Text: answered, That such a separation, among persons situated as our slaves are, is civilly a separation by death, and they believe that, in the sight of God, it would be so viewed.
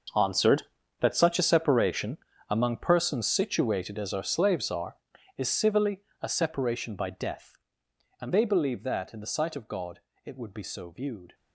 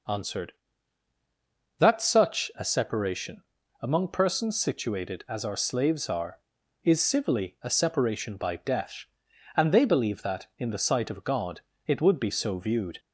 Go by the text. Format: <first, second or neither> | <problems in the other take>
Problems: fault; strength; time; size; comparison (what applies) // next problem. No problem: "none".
second | gets quieter; strong; throughout; 16 dB // pauses between "civilly" and "a"; slight; at 6.0 s; 0.18 s long